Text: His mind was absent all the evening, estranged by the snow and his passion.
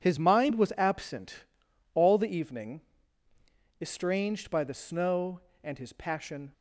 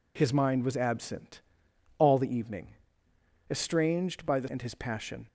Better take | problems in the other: first | pauses between "absent" and "all"; noticeable; at 1.4 s; 0.58 s long; noticeable in the first // skips "snow"; at 4.4 s

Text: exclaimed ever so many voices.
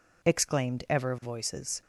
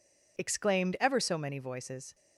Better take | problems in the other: second | skips "so many"; at 1.1 s

